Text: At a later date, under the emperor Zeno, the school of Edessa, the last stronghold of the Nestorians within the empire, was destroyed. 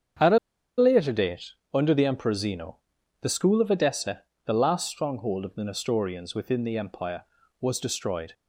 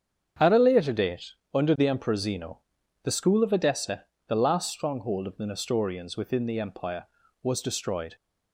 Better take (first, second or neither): second